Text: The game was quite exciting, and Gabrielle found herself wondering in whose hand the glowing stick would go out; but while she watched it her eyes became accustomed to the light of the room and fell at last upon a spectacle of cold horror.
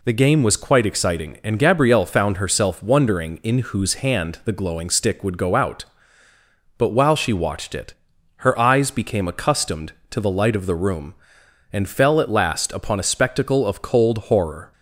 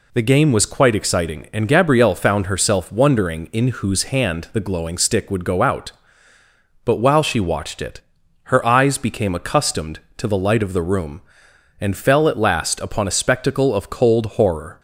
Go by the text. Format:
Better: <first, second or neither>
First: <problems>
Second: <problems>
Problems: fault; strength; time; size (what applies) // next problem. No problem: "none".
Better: neither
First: pauses between "it" and "her"; at 7.9 s; 0.44 s long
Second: pauses between "it" and "her"; at 7.9 s; 0.44 s long